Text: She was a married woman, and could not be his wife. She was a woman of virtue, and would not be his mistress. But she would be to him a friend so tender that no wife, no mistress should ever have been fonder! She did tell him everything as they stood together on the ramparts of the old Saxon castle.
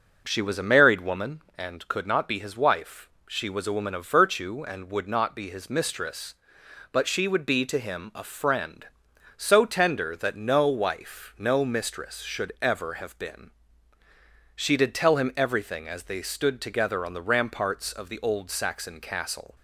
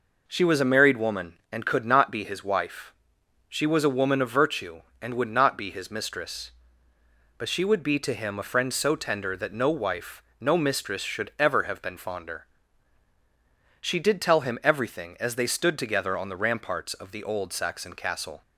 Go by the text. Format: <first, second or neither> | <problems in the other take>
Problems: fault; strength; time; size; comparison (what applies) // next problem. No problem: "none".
second | skips "fonder"; at 14.0 s